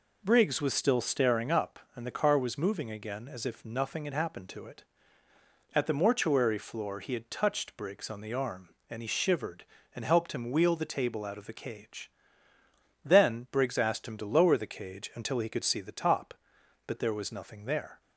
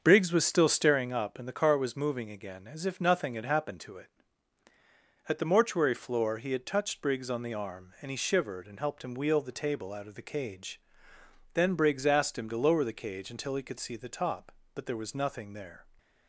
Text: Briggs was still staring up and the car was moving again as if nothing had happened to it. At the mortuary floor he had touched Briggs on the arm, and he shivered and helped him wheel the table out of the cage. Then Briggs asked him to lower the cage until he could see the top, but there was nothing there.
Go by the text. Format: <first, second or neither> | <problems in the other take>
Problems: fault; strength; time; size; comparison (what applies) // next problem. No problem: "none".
first | starts louder than the rest; until 1.1 s; 6.5 dB